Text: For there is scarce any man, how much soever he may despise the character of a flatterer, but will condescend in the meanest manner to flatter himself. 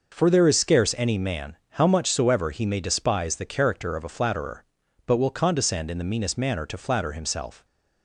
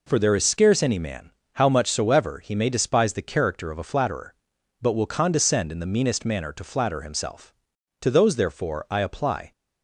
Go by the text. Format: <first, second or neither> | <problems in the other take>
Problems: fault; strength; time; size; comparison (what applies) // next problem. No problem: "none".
first | goes on to say "To those therefore I apply"; from 8.0 s on; 1.5 s long